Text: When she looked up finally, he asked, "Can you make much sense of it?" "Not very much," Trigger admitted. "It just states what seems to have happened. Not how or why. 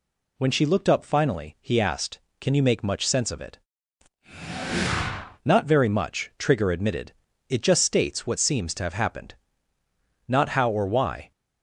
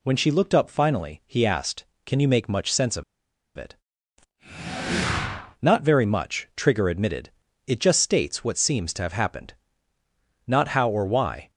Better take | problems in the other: first | pauses between "of" and "it"; noticeable; at 3.0 s; 0.54 s long

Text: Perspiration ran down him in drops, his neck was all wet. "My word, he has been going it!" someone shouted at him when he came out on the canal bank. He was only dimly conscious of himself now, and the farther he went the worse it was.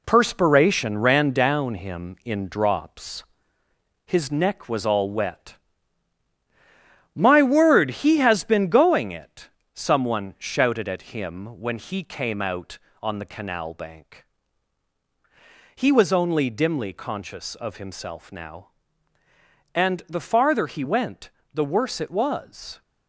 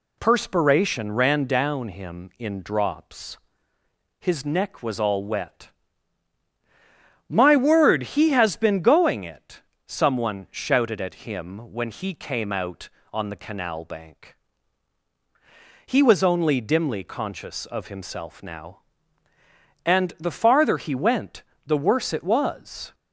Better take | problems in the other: second | gets quieter; throughout; 6.5 dB // pauses between "went" and "the"; slight; at 21.2 s; 0.24 s long; slight in the second

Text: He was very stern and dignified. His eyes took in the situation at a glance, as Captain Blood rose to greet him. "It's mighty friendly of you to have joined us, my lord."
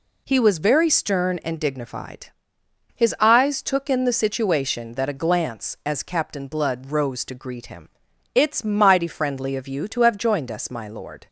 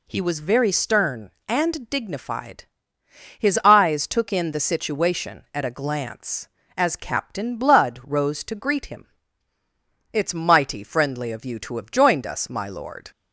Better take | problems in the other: second | says "that" for "at"; at 4.9 s

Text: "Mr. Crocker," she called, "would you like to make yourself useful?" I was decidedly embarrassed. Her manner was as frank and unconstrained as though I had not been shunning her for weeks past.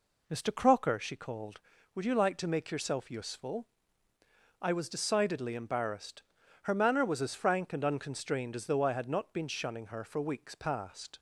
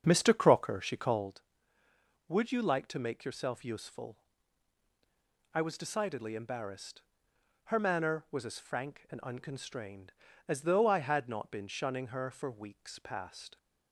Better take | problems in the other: first | starts louder than the rest; until 1.4 s; 7 dB

